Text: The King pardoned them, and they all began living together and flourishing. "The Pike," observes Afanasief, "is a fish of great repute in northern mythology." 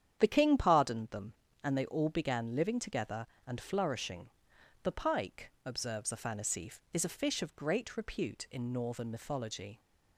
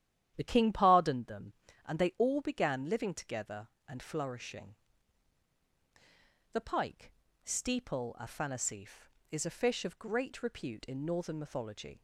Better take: first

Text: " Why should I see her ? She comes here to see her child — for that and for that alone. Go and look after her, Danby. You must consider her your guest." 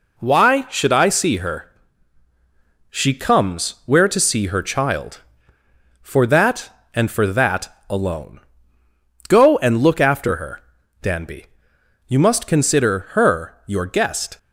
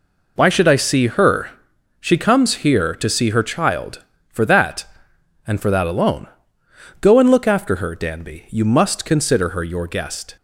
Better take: second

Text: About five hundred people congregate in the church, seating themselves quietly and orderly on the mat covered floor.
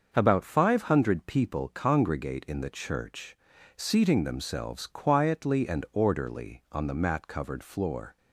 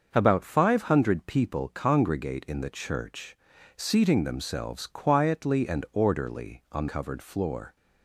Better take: first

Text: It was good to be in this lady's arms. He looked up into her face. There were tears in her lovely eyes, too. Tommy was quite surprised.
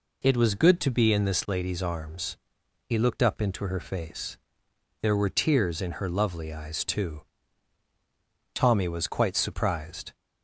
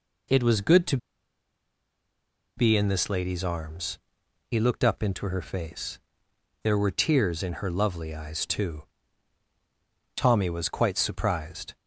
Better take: first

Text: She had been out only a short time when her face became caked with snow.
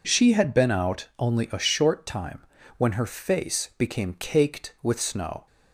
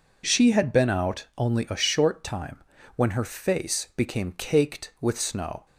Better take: neither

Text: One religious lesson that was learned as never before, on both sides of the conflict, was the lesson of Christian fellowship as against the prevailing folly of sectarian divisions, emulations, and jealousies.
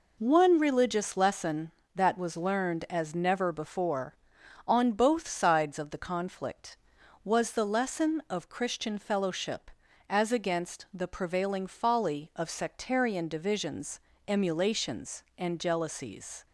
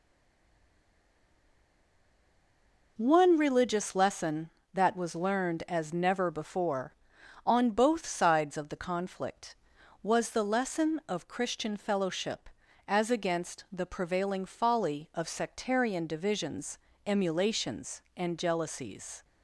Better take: first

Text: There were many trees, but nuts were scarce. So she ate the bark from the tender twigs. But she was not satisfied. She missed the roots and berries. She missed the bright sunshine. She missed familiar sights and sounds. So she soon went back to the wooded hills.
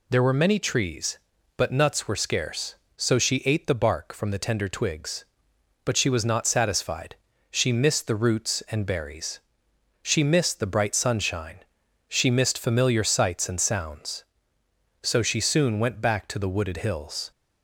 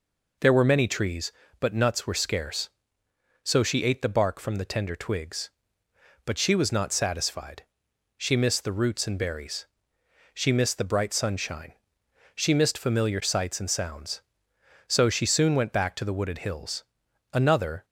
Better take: first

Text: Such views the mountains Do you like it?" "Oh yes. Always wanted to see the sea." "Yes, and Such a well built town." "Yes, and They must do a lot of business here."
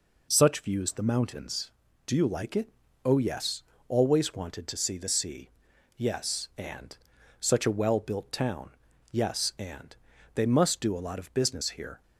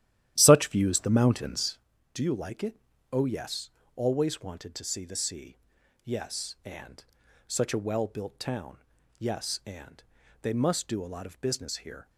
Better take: first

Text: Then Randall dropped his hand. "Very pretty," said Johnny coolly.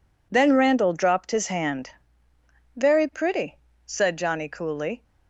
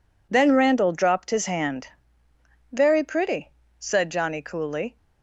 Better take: neither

